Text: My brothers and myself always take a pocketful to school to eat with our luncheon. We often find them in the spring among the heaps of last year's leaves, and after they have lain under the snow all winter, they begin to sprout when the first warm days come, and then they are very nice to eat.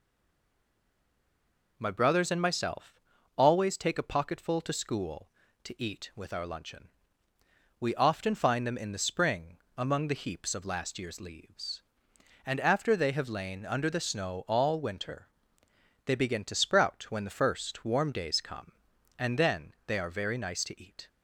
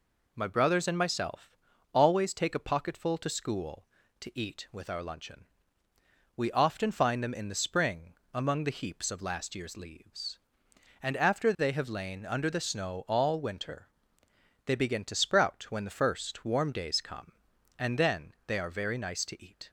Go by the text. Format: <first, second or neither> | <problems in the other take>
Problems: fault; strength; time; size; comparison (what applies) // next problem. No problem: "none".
second | stays silent before the first word; noticeable; until 1.7 s; 1.7 s long // pauses between "myself" and "always"; at 2.9 s; 0.42 s long; also in the second // pauses between "spring" and "among"; slight; at 9.5 s; 0.18 s long; slight in the second // pauses between "then" and "they"; slight; at 19.7 s; 0.16 s long; slight in the second